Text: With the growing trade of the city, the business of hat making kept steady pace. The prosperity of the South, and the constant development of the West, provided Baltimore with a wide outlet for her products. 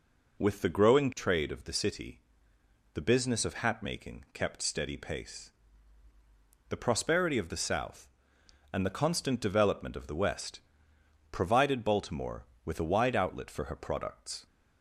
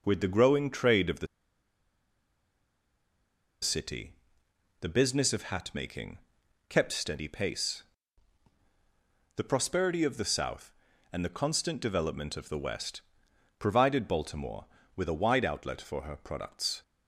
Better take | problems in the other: first | pauses between "the" and "city"; strong; at 1.2 s; 2.3 s long // pauses between "making" and "kept"; noticeable; at 6.1 s; 0.54 s long

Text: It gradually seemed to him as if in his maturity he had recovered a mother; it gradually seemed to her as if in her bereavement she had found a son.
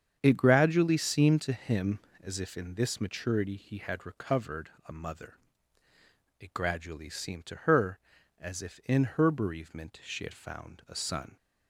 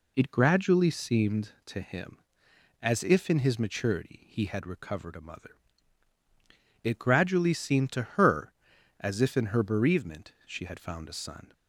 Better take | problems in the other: second | starts louder than the rest; strong; until 1.2 s; 7.5 dB // says "this" for "his"; at 2.7 s // pauses between "recovered" and "a"; slight; at 4.6 s; 0.16 s long

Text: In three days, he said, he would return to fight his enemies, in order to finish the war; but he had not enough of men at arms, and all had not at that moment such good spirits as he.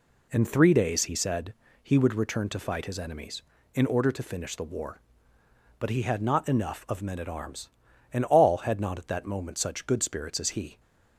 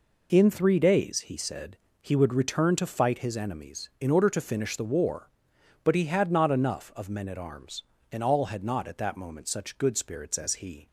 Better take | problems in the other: neither | none

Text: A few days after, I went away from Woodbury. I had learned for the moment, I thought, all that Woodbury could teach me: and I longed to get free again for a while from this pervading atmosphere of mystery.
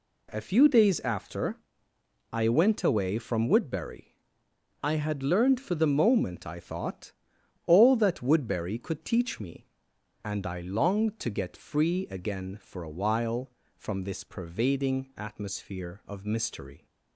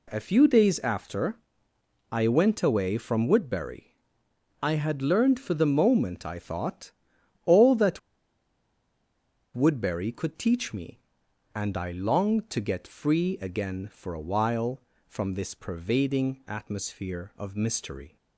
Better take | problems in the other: first | pauses between "that" and "Woodbury"; strong; at 7.9 s; 1.5 s long

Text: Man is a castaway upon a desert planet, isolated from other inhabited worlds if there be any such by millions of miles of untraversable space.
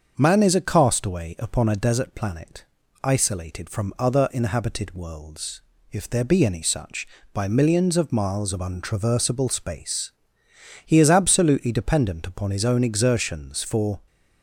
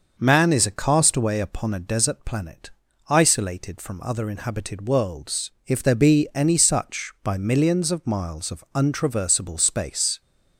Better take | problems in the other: second | starts louder than the rest; until 1.1 s; 6.5 dB; also in the second // pauses between "worlds" and "if"; slight; at 5.5 s; 0.30 s long; slight in the second // goes on to say "He is absolutely dependent upon his own exertions for"; strong; from 10.8 s on; 3.1 s long

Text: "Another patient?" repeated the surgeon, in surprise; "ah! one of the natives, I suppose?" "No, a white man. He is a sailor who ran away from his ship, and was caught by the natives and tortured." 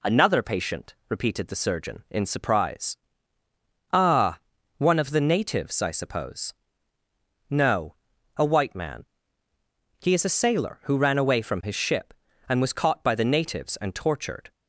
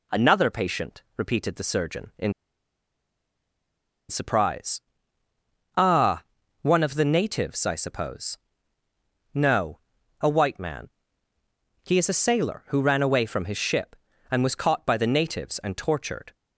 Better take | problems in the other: first | pauses between "in" and "surprise"; strong; at 2.3 s; 1.7 s long

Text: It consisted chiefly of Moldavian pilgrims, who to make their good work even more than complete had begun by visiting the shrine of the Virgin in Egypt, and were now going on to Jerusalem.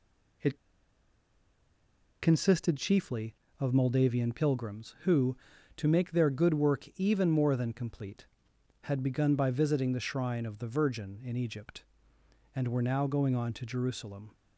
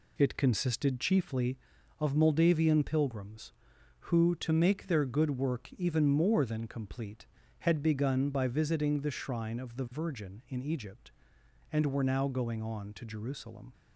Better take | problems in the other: second | pauses between "It" and "consisted"; strong; at 0.5 s; 1.6 s long

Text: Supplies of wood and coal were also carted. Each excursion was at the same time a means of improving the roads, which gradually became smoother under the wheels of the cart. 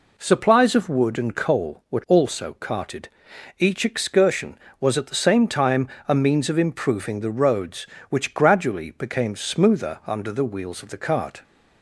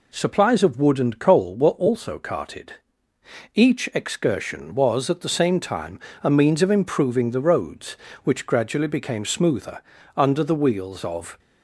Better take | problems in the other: first | pauses between "time" and "a"; slight; at 5.9 s; 0.24 s long; slight in the first // pauses between "smoother" and "under"; at 9.8 s; 0.38 s long // stops before "the cart"; at 11.3 s

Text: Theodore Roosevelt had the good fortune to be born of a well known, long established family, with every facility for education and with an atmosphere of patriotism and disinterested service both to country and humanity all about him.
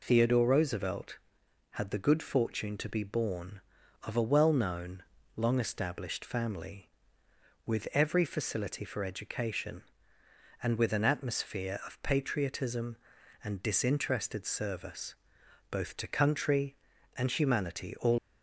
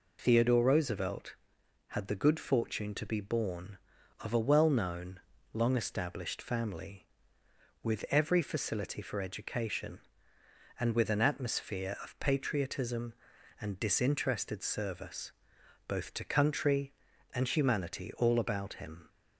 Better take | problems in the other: second | pauses between "service" and "both"; noticeable; at 15.1 s; 0.56 s long; noticeable in the second // stops before "about him"; at 18.1 s

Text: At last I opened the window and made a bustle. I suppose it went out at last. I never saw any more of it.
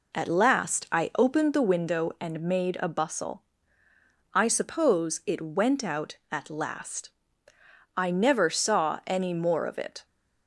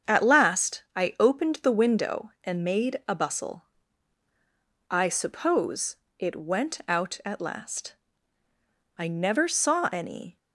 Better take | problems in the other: first | starts louder than the rest; strong; until 1.2 s; 7 dB // pauses between "suppose" and "it"; slight; at 5.9 s; 0.24 s long // stops before "more of it"; at 10.3 s

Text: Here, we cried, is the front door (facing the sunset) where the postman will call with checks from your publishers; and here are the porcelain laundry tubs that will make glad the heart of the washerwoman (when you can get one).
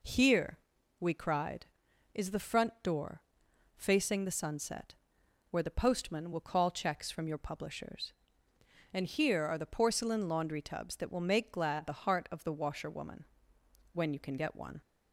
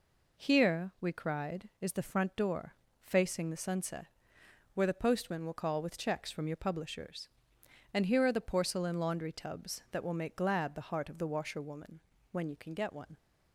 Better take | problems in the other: second | skips "with"; at 6.7 s

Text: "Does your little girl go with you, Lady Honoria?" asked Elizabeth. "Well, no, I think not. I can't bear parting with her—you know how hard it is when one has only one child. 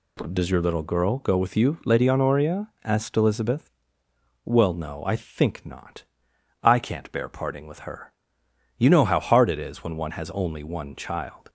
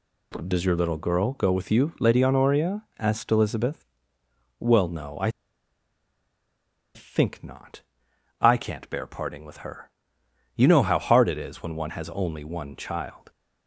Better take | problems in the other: first | pauses between "I" and "think"; strong; at 5.2 s; 1.6 s long

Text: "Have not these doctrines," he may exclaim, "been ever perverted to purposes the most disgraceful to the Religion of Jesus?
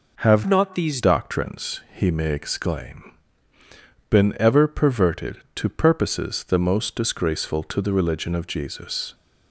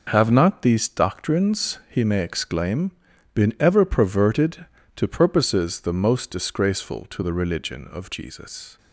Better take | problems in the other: second | changes voice from "not" to "these"; from 0.4 to 0.9 s; 0.5 s long

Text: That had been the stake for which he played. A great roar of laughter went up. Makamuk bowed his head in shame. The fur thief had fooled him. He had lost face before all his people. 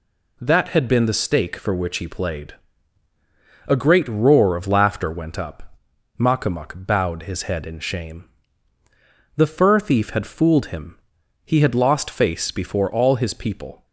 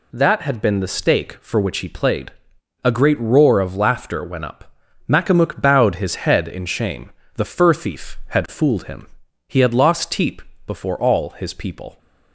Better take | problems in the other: first | says "teep" for "face"; at 10.1 s

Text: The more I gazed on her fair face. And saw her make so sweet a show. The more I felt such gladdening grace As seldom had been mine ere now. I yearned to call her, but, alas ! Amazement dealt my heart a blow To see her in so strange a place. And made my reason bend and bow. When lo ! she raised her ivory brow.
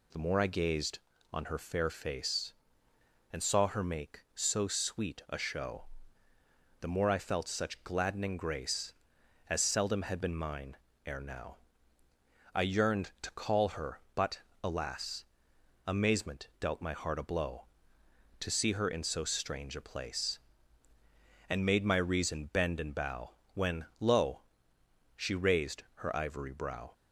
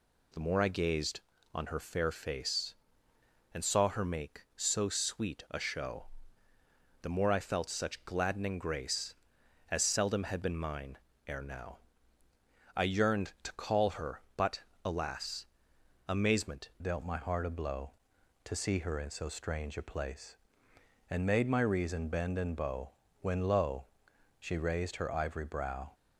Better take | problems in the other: first | pauses between "mine" and "ere"; slight; at 10.9 s; 0.30 s long; slight in the first // changes voice at "dealt"; from 16.8 s on; 9.1 s long

